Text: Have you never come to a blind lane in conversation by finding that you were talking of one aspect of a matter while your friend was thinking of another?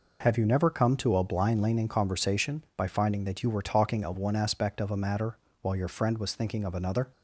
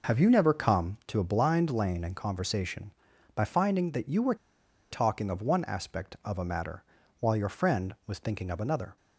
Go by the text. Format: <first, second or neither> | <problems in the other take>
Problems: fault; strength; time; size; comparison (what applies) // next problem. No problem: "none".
first | pauses between "were" and "talking"; noticeable; at 4.3 s; 0.56 s long // pauses between "matter" and "while"; at 6.8 s; 0.38 s long; slight in the first